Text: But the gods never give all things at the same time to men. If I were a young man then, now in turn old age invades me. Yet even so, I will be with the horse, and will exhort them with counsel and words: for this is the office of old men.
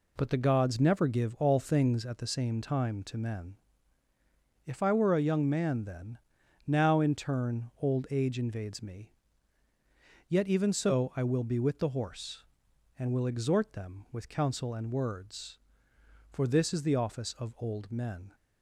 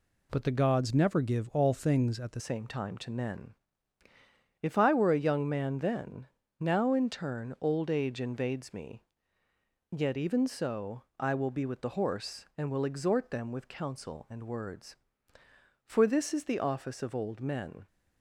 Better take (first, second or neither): first